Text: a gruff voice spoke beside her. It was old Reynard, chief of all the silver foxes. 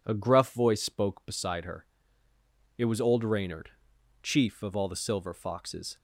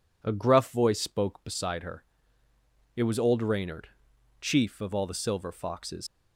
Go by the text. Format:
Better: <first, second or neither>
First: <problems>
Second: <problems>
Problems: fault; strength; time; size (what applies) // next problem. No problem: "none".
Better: first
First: none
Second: leaves "foxes" unfinished; at 6.0 s; 80 ms